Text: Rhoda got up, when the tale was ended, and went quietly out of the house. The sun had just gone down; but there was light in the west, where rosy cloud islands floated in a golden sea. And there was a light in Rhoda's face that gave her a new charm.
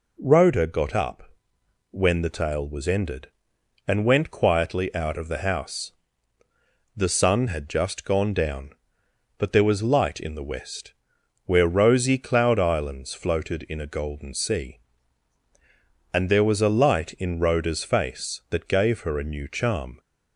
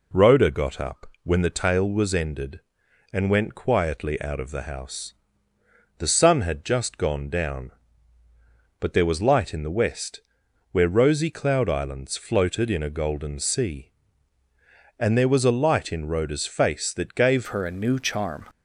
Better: first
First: none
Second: changes voice at "her"; from 17.4 s on; 1.0 s long

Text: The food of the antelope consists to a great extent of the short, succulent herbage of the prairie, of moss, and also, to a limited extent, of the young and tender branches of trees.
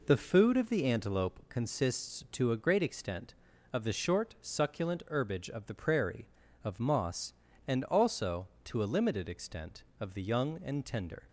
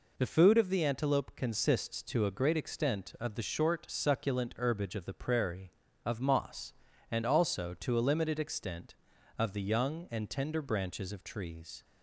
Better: second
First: stops before "branches of trees"; at 11.2 s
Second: none

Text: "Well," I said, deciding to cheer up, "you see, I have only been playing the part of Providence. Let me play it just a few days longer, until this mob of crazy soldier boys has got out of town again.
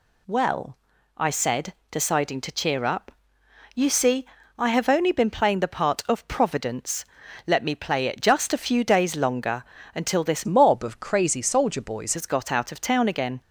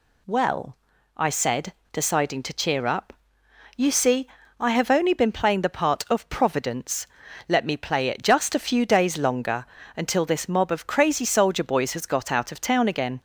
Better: second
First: changes voice from "mob" to "boys"; from 10.4 to 12.1 s; 1.7 s long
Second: none

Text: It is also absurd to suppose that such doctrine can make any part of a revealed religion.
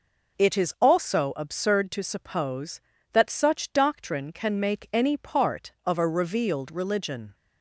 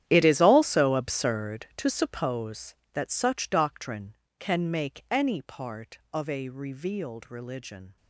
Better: first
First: none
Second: gets quieter; strong; throughout; 17 dB

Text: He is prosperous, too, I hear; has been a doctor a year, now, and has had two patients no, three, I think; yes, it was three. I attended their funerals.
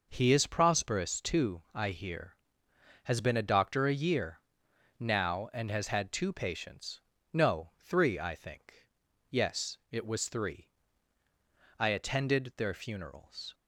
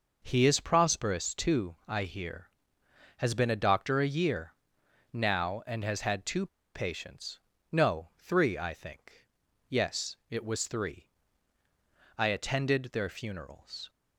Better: first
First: pauses between "patients" and "no"; slight; at 7.0 s; 0.30 s long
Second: pauses between "two" and "patients"; slight; at 6.4 s; 0.28 s long // pauses between "patients" and "no"; slight; at 7.3 s; 0.30 s long

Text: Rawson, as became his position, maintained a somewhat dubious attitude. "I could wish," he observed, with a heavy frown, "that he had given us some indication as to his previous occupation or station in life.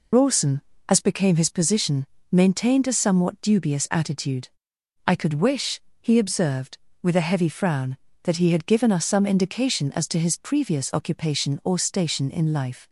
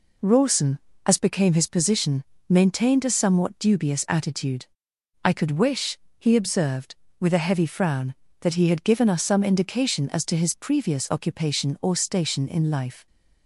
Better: second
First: loses the start of "Rawson"; at 0.1 s; 100 ms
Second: none

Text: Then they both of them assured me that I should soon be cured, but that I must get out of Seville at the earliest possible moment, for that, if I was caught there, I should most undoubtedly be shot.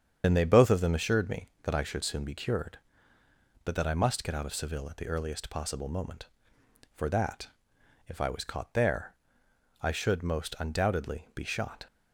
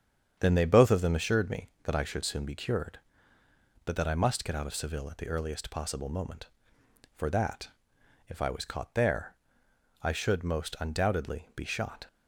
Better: second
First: loses the start of "Then"; at 0.2 s; 55 ms // starts louder than the rest; strong; until 1.2 s; 8 dB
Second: starts louder than the rest; strong; until 1.4 s; 8 dB

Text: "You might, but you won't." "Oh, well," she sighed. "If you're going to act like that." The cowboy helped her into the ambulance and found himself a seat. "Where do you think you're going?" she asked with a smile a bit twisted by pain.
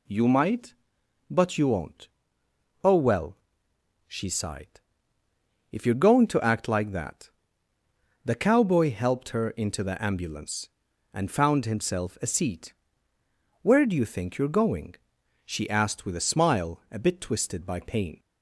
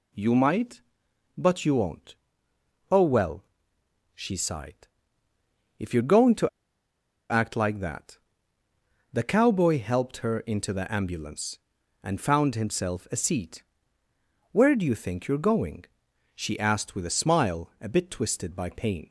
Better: first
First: none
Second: pauses between "to" and "act"; noticeable; at 6.4 s; 0.83 s long

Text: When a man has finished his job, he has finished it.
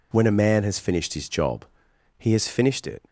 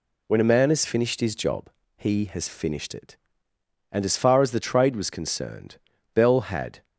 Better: first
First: none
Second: goes on to say "And as far as the Trade was concerned Bell had"; strong; from 3.9 s on; 2.9 s long

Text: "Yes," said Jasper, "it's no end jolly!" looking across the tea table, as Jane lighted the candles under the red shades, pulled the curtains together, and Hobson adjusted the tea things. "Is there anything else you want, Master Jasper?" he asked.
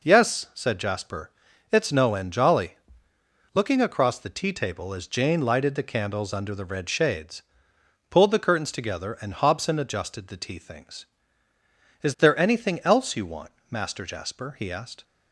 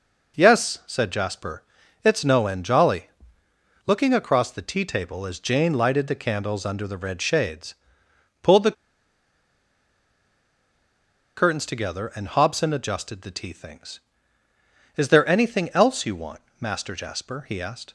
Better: first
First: none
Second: pauses between "the" and "curtains"; strong; at 8.7 s; 2.6 s long

